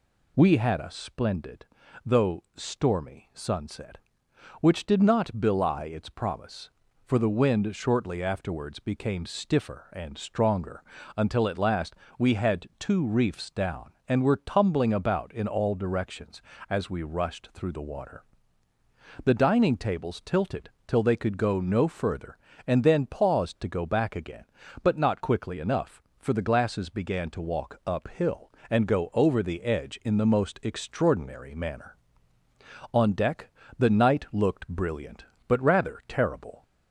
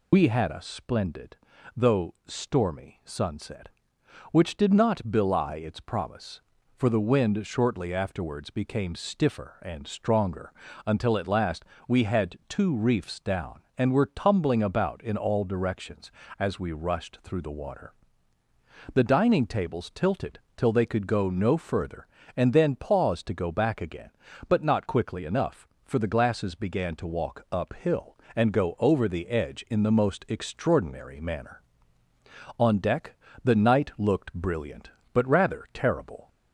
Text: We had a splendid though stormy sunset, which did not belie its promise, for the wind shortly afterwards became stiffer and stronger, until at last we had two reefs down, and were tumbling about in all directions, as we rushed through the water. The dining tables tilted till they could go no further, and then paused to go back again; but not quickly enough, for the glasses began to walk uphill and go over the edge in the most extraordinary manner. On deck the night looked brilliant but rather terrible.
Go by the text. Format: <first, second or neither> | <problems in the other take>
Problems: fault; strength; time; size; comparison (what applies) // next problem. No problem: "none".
first | loses the start of "We"; at 0.1 s; 50 ms // pauses between "splendid" and "though"; at 1.3 s; 0.40 s long; also in the first // pauses between "last" and "we"; slight; at 11.6 s; 0.22 s long; slight in the first // pauses between "tilted" and "till"; slight; at 20.4 s; 0.16 s long; slight in the first // pauses between "deck" and "the"; slight; at 33.1 s; 0.26 s long; slight in the first